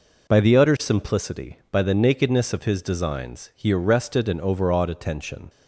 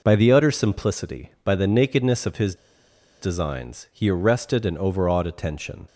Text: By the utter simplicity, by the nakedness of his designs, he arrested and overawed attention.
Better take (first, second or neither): first